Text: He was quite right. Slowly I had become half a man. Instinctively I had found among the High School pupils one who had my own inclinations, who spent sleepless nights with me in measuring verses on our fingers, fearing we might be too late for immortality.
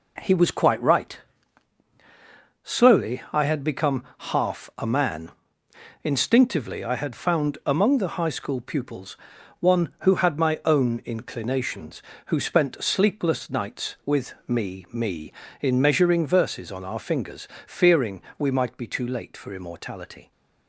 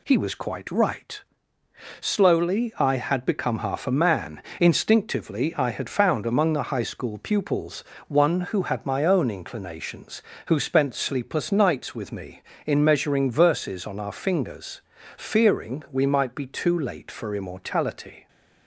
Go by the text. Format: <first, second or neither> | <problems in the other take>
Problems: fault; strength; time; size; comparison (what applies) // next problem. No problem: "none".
second | pauses between "pupils" and "one"; at 9.1 s; 0.42 s long; slight in the second // says "me" twice; at 14.9 s // pauses between "fearing" and "we"; slight; at 18.2 s; 0.16 s long